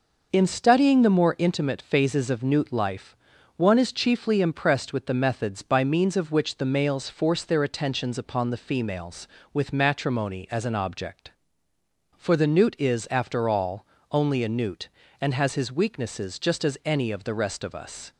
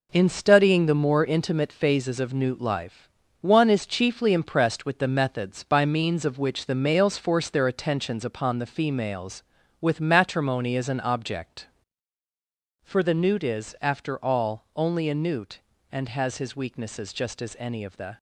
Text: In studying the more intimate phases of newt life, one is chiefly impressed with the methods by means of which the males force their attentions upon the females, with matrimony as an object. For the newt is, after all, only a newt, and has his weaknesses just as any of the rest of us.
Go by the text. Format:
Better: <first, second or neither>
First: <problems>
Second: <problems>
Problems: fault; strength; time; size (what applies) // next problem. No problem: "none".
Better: first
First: none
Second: stops before "rest of us"; at 18.1 s